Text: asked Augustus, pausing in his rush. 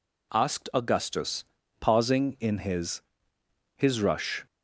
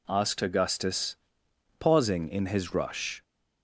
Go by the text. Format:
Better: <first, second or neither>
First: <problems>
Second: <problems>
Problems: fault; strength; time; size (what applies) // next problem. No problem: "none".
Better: second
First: says "his" twice; at 3.7 s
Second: none